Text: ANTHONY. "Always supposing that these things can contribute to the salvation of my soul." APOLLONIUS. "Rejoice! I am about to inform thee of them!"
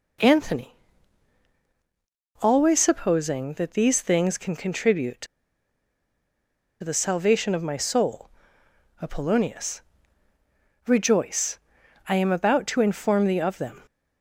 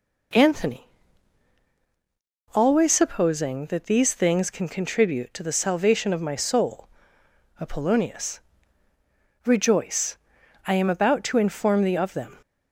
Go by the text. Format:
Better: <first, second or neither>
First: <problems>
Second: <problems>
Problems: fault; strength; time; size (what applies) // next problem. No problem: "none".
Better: second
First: pauses between "to" and "the"; strong; at 5.2 s; 1.5 s long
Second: none